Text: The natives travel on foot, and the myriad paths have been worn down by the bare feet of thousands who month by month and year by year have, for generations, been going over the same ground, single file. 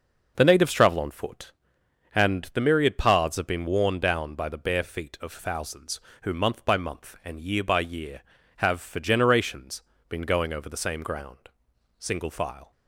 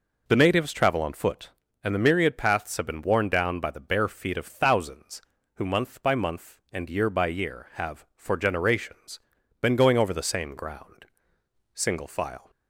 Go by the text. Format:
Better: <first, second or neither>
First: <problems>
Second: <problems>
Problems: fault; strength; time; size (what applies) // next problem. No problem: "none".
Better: neither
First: none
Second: none